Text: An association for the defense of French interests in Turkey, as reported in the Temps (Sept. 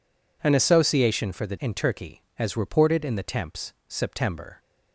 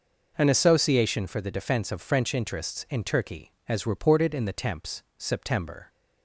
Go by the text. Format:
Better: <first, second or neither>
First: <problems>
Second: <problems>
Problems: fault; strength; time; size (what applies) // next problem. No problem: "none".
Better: second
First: skips "defense of French interests"; at 1.5 s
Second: none